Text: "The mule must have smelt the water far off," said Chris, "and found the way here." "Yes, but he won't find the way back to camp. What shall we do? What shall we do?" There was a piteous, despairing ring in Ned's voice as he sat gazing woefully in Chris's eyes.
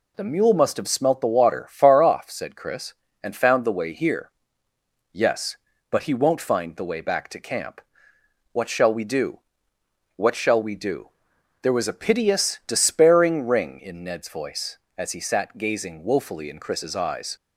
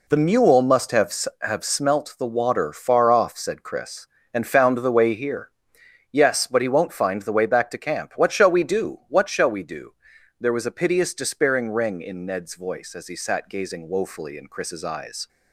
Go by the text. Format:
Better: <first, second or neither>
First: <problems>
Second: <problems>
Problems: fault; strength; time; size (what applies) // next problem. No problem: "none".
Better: first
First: none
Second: says "have" twice; at 1.4 s